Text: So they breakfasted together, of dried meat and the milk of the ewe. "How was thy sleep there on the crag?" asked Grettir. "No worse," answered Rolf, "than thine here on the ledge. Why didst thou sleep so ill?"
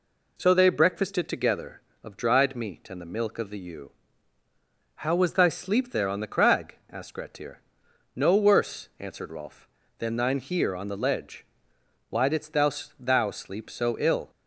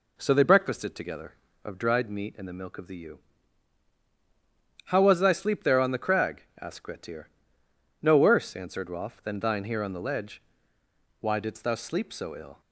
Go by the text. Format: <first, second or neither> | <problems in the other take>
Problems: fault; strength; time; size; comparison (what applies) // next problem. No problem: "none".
second | says "thou" twice; at 13.0 s